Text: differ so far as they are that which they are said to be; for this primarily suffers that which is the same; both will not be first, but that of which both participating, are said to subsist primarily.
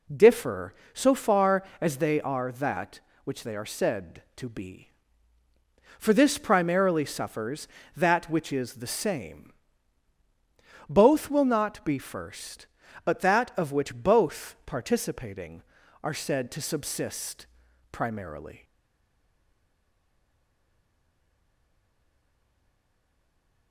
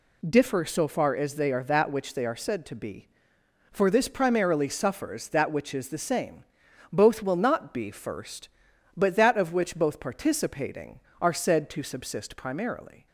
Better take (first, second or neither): second